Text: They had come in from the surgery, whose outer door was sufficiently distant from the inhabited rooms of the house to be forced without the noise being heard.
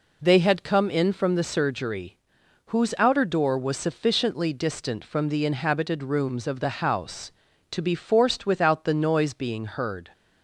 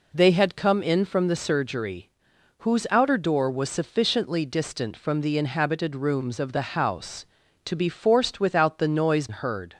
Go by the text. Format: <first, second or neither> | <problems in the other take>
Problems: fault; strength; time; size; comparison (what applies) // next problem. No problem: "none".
first | skips "being"; at 9.2 s